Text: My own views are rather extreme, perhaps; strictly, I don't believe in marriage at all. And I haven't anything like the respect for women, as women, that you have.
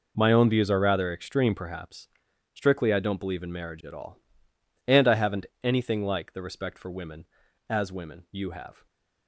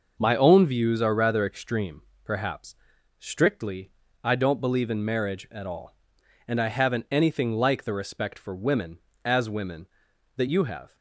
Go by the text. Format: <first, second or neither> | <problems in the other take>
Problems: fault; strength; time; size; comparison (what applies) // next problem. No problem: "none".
second | pauses between "haven't" and "anything"; slight; at 5.4 s; 0.16 s long // skips "that"; at 8.2 s // stays silent after the last word; slight; from 8.7 s on; 0.5 s long